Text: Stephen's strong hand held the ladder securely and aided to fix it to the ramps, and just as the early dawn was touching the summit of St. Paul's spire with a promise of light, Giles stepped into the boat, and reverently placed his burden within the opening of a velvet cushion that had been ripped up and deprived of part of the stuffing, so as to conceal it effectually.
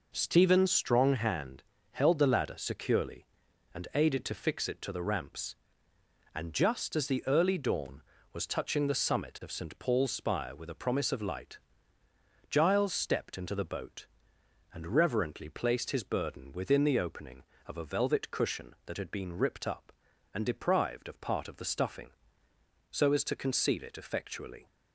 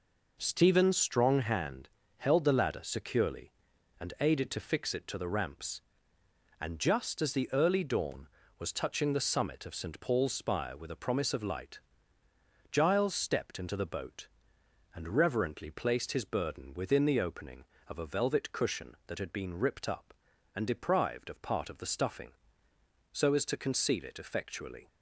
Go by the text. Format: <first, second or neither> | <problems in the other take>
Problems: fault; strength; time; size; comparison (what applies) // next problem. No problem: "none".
neither | pauses between "hand" and "held"; slight; the same in both